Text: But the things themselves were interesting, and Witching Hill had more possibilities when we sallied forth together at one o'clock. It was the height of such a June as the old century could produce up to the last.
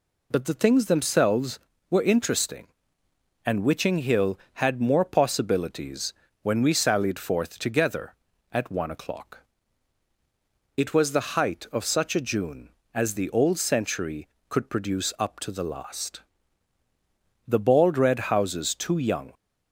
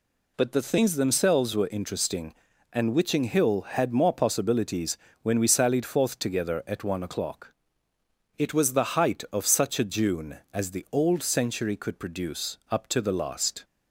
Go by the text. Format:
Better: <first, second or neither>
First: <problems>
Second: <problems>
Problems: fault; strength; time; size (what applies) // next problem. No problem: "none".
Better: second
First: pauses between "possibilities" and "when"; slight; at 6.1 s; 0.28 s long // goes on to say "The bald red houses too young"; strong; from 17.4 s on; 1.8 s long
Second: pauses between "possibilities" and "when"; slight; at 4.9 s; 0.24 s long